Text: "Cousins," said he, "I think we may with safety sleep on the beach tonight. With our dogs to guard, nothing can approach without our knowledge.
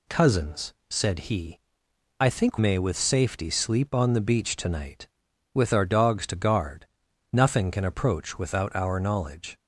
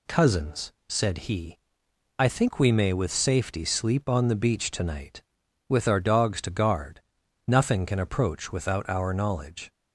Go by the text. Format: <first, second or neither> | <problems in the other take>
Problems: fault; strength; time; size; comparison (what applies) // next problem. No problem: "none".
second | skips "we"; at 2.5 s